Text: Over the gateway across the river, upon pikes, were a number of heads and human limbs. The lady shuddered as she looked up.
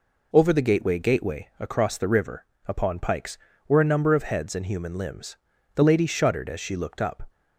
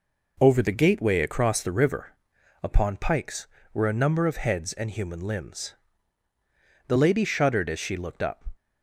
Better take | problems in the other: second | says "gateway" twice; at 0.9 s

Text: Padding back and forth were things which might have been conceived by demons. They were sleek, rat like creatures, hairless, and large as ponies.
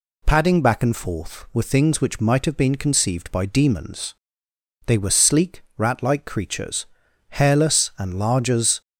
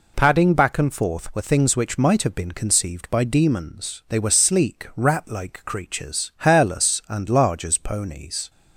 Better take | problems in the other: second | stops before "ponies"; at 8.8 s

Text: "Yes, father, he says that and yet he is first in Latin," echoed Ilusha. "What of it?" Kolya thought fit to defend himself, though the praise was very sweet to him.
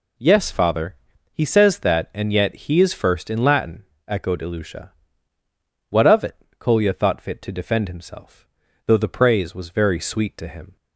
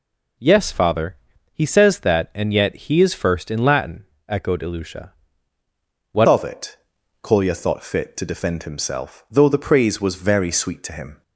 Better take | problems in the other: first | changes voice at "of"; from 6.2 s on; 5.0 s long

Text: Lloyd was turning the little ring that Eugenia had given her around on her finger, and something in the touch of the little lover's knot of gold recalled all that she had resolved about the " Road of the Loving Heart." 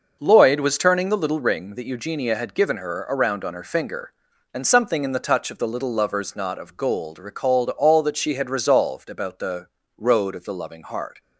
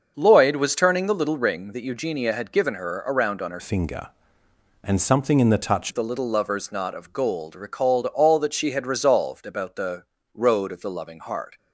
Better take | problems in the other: first | starts louder than the rest; until 1.1 s; 6.5 dB // changes voice from "finger" to "touch"; from 3.5 to 5.9 s; 2.4 s long

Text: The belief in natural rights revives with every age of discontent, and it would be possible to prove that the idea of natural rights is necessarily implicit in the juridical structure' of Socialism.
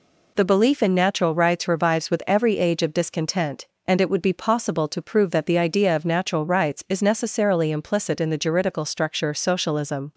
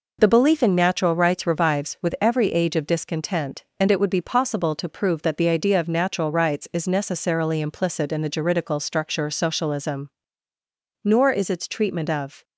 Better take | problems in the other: first | goes on to say "Nor is its treatment of"; from 11.0 s on; 1.3 s long

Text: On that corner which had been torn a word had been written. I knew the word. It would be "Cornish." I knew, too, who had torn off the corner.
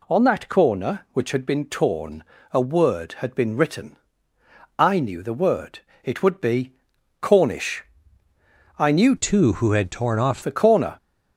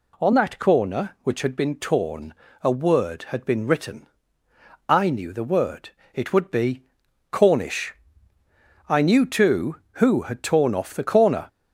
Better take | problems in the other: second | pauses between "torn" and "a"; slight; at 2.2 s; 0.28 s long; slight in the second // pauses between "be" and "Cornish"; noticeable; at 6.7 s; 0.48 s long; noticeable in the second // changes voice from "too" to "off"; from 9.1 to 10.4 s; 1.3 s long

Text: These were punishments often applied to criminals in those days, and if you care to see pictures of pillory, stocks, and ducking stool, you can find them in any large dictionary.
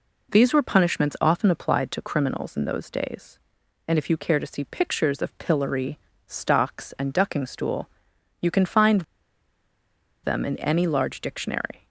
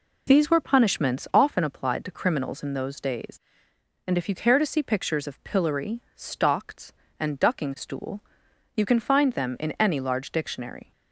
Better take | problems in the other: second | pauses between "find" and "them"; at 9.0 s; 1.2 s long

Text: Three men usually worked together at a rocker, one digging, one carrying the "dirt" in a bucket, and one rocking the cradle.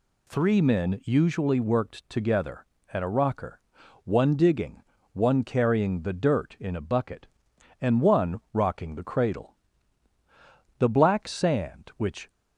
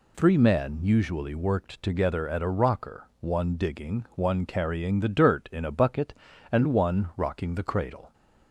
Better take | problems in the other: second | goes on to say "The black sand which"; from 10.7 s on; 1.5 s long

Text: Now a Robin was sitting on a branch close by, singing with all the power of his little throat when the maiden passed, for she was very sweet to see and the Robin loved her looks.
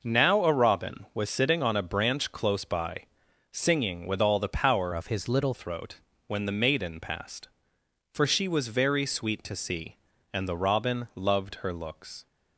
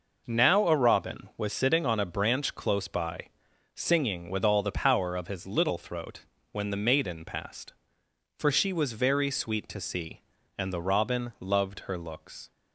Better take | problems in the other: second | changes voice from "of" to "little"; from 4.9 to 5.5 s; 0.6 s long // pauses between "throat" and "when"; slight; at 6.0 s; 0.26 s long; slight in the second

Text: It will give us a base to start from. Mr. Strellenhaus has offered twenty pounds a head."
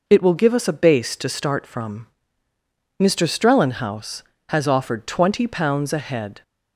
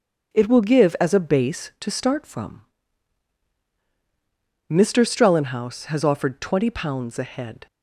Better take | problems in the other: first | starts louder than the rest; strong; until 1.3 s; 8 dB // says "as" for "us"; at 0.9 s

